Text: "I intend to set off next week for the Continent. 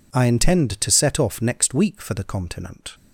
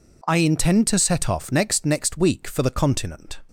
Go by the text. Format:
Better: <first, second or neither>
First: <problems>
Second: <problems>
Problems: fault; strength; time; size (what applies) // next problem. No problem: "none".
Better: first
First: none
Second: says "next" twice; at 1.8 s